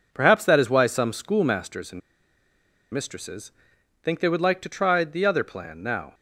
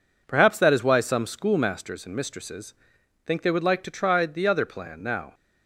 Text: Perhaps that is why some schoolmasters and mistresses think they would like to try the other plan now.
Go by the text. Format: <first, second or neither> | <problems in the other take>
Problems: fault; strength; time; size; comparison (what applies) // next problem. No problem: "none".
second | pauses between "and" and "mistresses"; noticeable; at 2.0 s; 0.93 s long // pauses between "mistresses" and "think"; noticeable; at 3.5 s; 0.52 s long; noticeable in the second